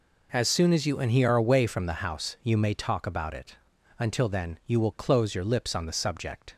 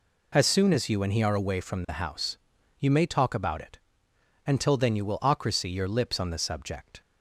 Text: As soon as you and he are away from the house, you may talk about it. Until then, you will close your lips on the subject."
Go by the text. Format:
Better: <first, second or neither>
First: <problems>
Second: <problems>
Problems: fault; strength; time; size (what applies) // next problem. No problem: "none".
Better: first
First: none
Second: says "ocracy" for "close"; at 5.2 s